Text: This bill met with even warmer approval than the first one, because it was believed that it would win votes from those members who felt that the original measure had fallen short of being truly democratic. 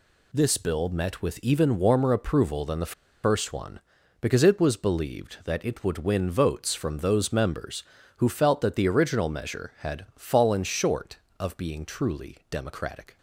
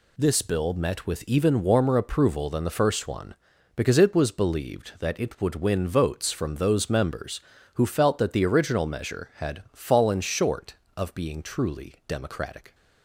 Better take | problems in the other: second | pauses between "the" and "first"; slight; at 2.9 s; 0.30 s long

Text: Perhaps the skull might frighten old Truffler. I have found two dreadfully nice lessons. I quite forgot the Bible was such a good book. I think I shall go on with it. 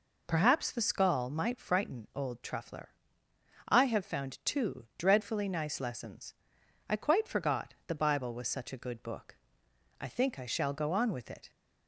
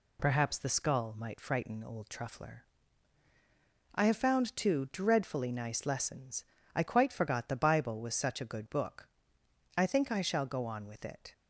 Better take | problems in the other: neither | none

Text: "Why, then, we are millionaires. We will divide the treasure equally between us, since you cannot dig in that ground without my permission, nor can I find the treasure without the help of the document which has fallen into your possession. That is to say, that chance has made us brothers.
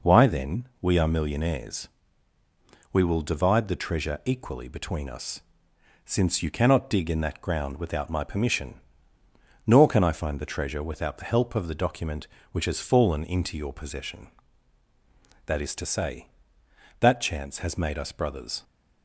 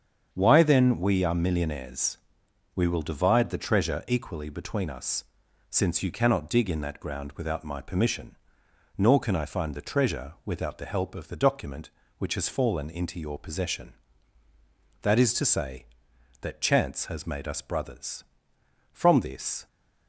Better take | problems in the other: first | starts louder than the rest; strong; until 1.3 s; 7.5 dB // goes on to say "From this"; noticeable; from 18.9 s on; 0.74 s long

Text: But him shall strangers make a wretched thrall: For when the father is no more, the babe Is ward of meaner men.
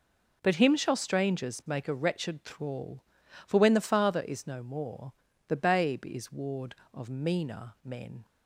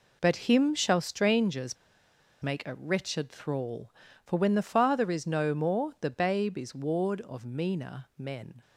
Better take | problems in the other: first | pauses between "strangers" and "make"; noticeable; at 1.7 s; 0.66 s long

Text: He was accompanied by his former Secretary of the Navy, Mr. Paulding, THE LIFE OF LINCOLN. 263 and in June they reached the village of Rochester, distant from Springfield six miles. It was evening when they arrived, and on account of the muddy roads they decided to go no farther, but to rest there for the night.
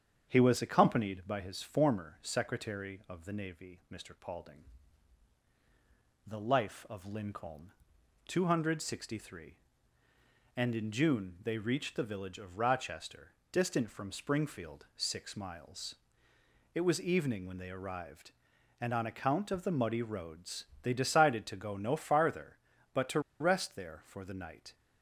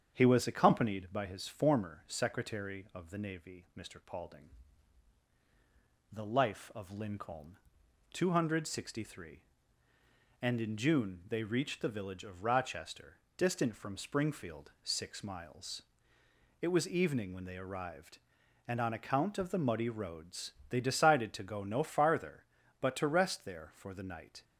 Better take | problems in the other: second | starts louder than the rest; strong; until 1.3 s; 8 dB; strong in the second // pauses between "roads" and "they"; slight; at 20.6 s; 0.16 s long; slight in the second // pauses between "to" and "rest"; slight; at 23.2 s; 0.19 s long

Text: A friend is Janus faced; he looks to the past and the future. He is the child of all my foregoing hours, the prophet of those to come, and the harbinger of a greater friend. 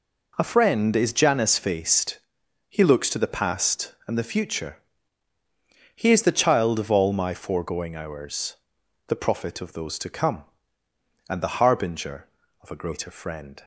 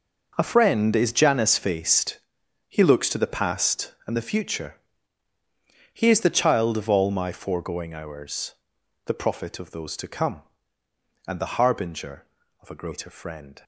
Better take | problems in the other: first | gets quieter; strong; throughout; 12.5 dB

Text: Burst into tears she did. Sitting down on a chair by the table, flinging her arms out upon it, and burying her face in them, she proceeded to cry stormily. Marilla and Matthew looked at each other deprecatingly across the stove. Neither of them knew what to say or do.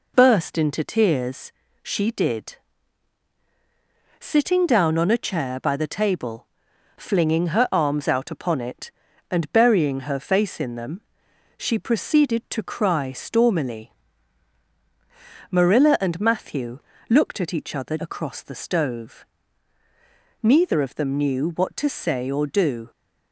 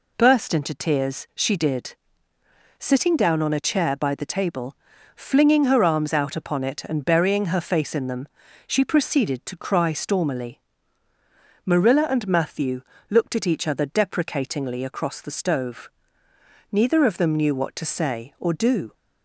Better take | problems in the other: second | pauses between "tears" and "she"; slight; at 1.5 s; 0.32 s long // pauses between "Matthew" and "looked"; slight; at 16.7 s; 0.30 s long; slight in the second // skips "deprecatingly"; at 17.9 s

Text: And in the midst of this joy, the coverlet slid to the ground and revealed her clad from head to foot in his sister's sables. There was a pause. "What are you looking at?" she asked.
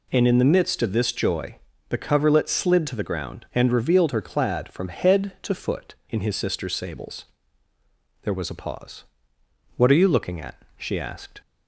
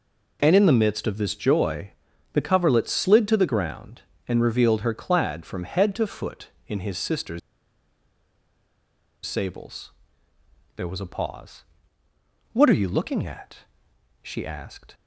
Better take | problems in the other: first | pauses between "sister's" and "sables"; strong; at 7.3 s; 1.8 s long

